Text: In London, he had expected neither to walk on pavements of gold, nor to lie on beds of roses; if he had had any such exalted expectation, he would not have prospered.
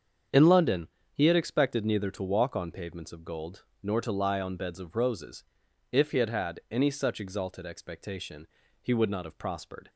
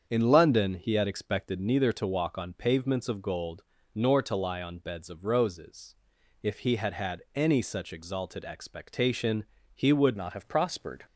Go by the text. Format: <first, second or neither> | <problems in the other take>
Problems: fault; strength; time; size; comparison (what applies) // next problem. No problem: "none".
first | starts louder than the rest; strong; until 1.1 s; 7.5 dB; strong in the first // changes voice at "not"; from 10.1 s on; 0.9 s long